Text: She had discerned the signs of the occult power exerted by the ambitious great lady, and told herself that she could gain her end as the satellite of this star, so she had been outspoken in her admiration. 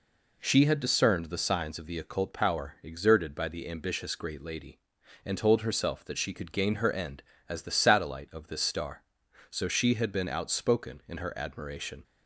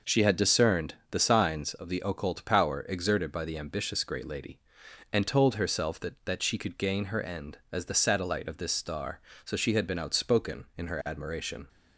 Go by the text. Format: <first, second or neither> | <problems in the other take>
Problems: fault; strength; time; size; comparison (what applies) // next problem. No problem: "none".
first | pauses between "discerned" and "the"; slight; at 0.9 s; 0.18 s long // says "that" twice; at 6.2 s